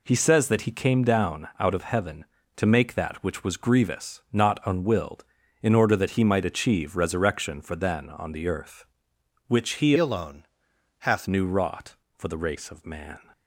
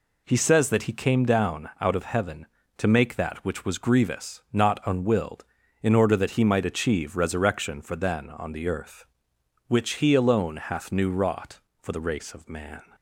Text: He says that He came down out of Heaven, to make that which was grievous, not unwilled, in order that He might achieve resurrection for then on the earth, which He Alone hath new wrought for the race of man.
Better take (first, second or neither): second